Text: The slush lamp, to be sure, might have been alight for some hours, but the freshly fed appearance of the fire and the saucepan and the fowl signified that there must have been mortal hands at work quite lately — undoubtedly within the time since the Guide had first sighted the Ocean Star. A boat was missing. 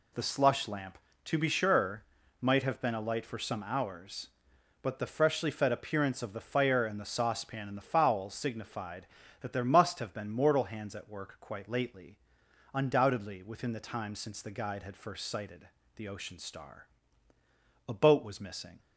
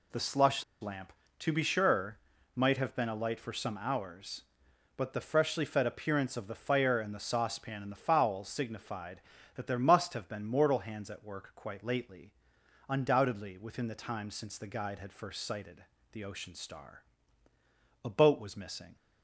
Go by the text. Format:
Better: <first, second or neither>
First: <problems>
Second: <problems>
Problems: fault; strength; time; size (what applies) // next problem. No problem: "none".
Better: first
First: pauses between "sighted" and "the"; slight; at 15.6 s; 0.28 s long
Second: pauses between "slush" and "lamp"; slight; at 0.6 s; 0.19 s long // pauses between "sighted" and "the"; slight; at 15.8 s; 0.28 s long